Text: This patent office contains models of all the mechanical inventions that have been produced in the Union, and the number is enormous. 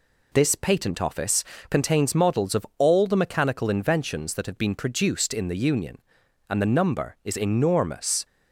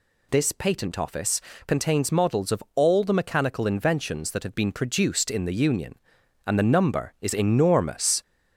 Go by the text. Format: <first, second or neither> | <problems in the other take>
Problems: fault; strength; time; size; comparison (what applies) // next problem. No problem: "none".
first | gets louder; slight; throughout; 2.5 dB // pauses between "office" and "contains"; slight; at 1.3 s; 0.26 s long; slight in the first